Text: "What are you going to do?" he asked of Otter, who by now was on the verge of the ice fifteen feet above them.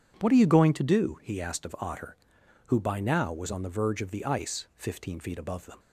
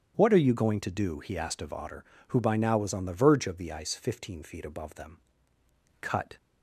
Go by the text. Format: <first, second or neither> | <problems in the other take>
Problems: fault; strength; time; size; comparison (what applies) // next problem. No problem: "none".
first | starts louder than the rest; strong; until 1.1 s; 8.5 dB // goes on to say "Cut"; slight; from 5.9 s on; 0.36 s long